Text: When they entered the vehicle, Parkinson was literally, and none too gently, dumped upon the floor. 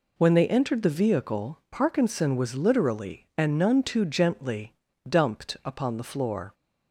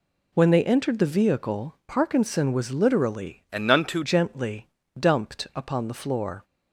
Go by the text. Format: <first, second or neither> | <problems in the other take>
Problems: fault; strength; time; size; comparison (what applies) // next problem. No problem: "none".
first | changes voice from "and" to "too"; from 3.5 to 4.0 s; 0.5 s long